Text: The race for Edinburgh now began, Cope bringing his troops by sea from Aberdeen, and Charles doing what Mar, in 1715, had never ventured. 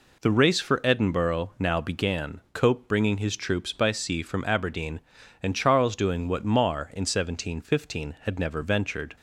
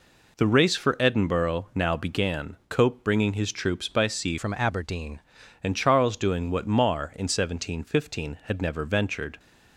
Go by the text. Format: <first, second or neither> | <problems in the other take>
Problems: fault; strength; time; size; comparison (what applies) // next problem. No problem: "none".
first | changes voice from "from" to "Aberdeen"; from 4.3 to 5.2 s; 0.9 s long